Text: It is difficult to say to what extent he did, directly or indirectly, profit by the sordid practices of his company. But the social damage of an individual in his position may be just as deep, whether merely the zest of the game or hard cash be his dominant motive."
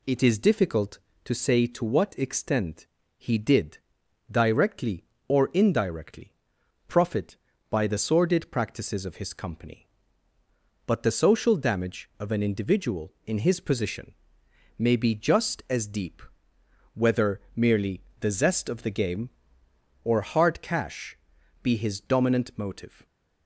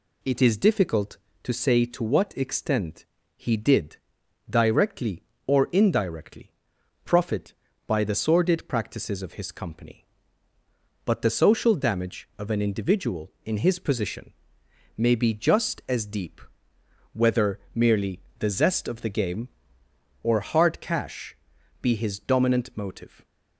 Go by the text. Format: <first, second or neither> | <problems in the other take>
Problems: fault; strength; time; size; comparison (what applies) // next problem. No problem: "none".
neither | pauses between "extent" and "he"; slight; the same in both // pauses between "position" and "may"; noticeable; the same in both // pauses between "whether" and "merely"; slight; the same in both // pauses between "merely" and "the"; slight; the same in both // pauses between "cash" and "be"; noticeable; the same in both